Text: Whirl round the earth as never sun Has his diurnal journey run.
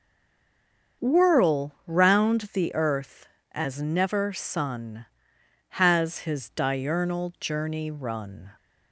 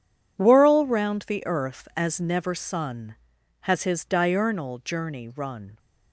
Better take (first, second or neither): second